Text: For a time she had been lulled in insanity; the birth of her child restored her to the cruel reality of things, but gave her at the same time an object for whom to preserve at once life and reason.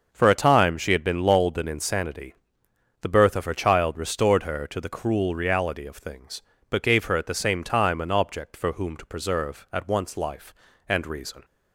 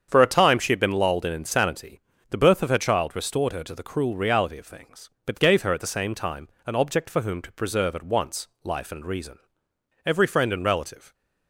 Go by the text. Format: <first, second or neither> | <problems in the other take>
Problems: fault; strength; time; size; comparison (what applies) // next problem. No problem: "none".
first | starts louder than the rest; strong; until 1.1 s; 7.5 dB; also in the first // pauses between "time" and "an"; slight; at 6.4 s; 0.18 s long // pauses between "once" and "life"; slight; at 8.4 s; 0.16 s long // goes on to say "Every friend and relative"; noticeable; from 10.0 s on; 1.0 s long